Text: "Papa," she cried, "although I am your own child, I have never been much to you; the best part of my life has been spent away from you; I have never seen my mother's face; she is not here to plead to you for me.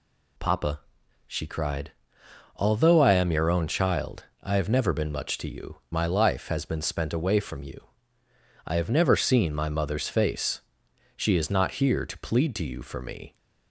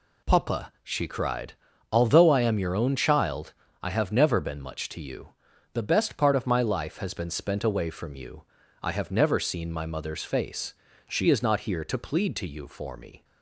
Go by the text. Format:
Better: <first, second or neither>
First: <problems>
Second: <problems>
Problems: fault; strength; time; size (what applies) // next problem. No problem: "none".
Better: second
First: skips "the best part of"; at 5.8 s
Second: none